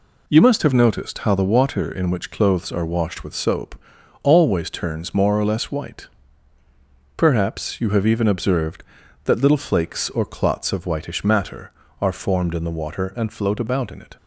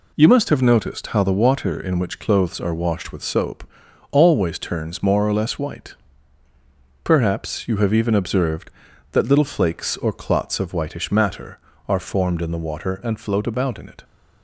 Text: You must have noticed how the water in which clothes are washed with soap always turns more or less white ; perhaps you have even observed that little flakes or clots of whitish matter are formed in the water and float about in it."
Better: neither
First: pauses between "soap" and "always"; noticeable; at 3.7 s; 0.48 s long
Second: pauses between "soap" and "always"; noticeable; at 3.6 s; 0.48 s long

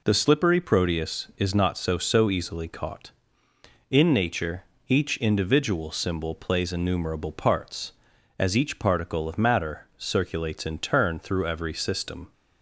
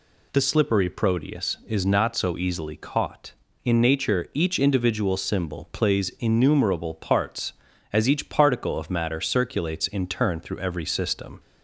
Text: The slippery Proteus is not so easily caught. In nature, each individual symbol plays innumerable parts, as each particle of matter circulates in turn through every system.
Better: second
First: says "so" twice; at 1.9 s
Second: none

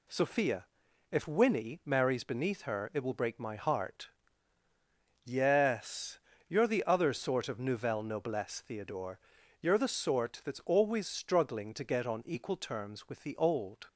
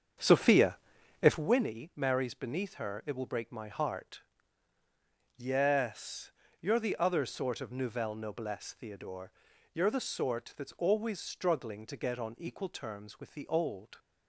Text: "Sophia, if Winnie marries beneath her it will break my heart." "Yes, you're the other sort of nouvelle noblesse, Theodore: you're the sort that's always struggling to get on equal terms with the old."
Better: first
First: none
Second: starts louder than the rest; strong; until 1.5 s; 7.5 dB

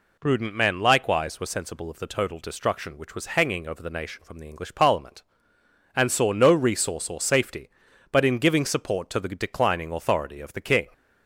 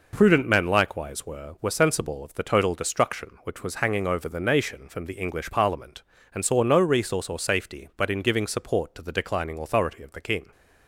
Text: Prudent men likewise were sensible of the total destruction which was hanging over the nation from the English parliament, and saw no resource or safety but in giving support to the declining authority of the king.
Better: first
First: none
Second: says "were" twice; at 1.5 s

